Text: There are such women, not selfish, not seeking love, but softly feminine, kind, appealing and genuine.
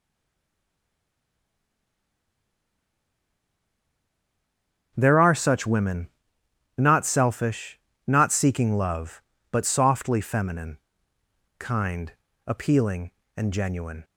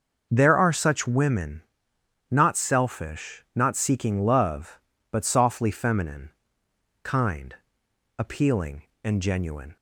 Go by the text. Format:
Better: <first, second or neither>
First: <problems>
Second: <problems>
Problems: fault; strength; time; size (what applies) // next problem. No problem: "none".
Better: second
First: stays silent before the first word; strong; until 4.9 s; 4.9 s long // starts louder than the rest; until 5.9 s; 7 dB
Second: starts louder than the rest; noticeable; until 1.3 s; 6 dB